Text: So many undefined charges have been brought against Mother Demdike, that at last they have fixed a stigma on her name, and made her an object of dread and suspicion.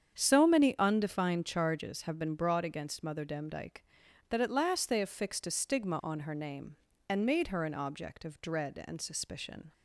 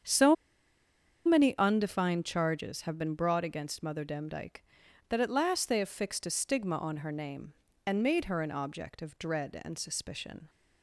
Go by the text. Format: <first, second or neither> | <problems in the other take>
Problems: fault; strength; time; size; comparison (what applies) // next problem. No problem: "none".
first | starts louder than the rest; strong; until 1.9 s; 7.5 dB; strong in the first // pauses between "So" and "many"; noticeable; at 0.3 s; 0.90 s long